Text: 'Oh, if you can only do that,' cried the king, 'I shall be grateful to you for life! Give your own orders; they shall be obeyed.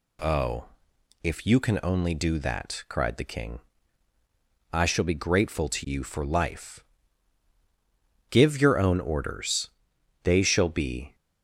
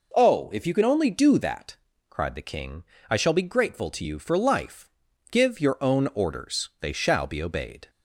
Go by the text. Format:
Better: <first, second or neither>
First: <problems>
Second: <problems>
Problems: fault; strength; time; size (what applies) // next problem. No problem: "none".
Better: second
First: stops before "obeyed"; at 11.1 s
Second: none